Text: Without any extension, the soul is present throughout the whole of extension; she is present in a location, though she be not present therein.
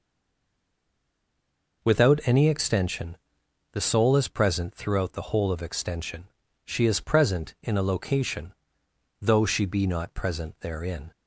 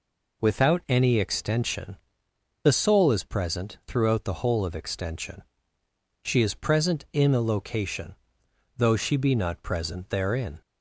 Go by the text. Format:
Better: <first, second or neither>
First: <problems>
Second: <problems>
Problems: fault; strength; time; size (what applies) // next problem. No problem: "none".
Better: second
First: stays silent before the first word; noticeable; until 1.8 s; 1.8 s long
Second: none